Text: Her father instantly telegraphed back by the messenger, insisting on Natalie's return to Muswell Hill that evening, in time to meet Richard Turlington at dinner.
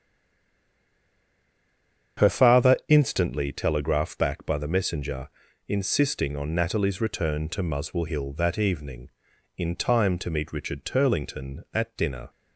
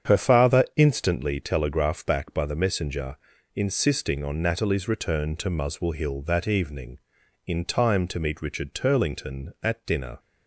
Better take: second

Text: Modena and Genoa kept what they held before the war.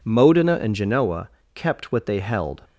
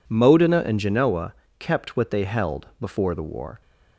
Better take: second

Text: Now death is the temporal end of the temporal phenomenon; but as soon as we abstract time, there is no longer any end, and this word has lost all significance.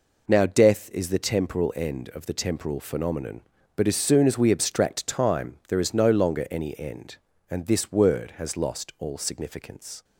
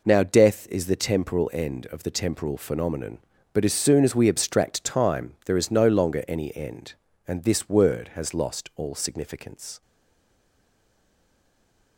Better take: first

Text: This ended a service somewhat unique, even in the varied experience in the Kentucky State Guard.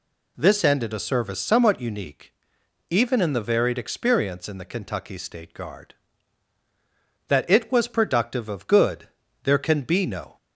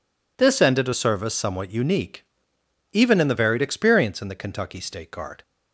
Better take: second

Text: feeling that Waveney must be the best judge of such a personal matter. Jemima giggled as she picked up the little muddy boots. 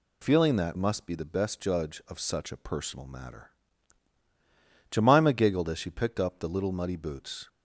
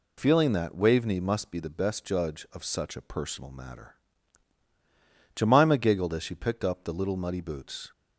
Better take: second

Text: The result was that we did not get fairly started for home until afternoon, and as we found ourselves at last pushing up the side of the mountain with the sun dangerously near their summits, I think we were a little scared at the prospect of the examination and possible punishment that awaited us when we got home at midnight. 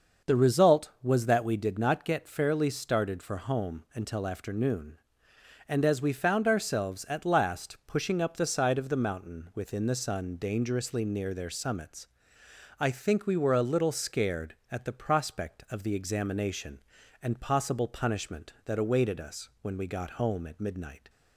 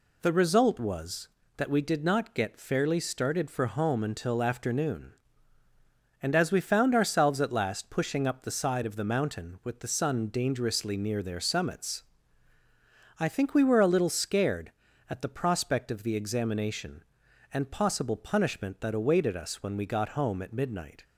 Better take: second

